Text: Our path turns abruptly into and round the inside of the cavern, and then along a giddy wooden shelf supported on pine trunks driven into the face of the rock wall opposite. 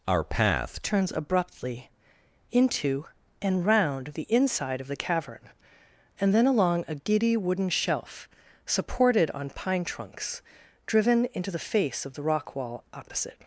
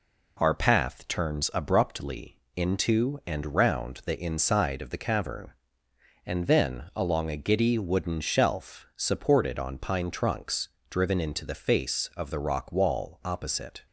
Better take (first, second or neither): second